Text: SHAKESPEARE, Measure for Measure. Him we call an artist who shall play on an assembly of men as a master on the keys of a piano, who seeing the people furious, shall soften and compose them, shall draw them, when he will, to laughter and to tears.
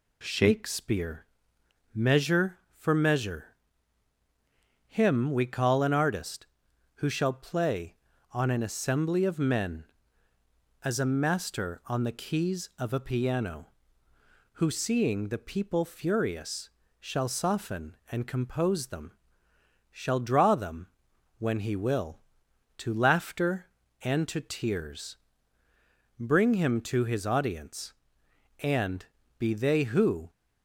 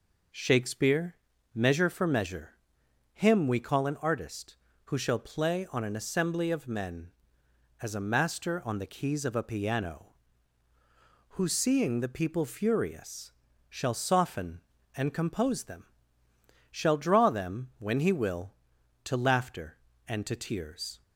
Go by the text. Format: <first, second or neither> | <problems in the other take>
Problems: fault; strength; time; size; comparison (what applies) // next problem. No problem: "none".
second | goes on to say "Bring him to his audience and be they who"; strong; from 26.1 s on; 4.1 s long